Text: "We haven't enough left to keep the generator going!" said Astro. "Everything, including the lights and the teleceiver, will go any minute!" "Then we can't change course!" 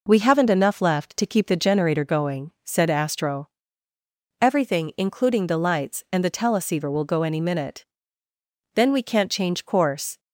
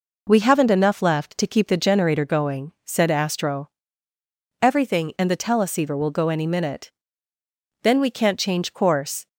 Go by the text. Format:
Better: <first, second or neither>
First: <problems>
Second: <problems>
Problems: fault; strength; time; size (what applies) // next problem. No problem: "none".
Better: first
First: none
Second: skips "including the lights"; at 5.1 s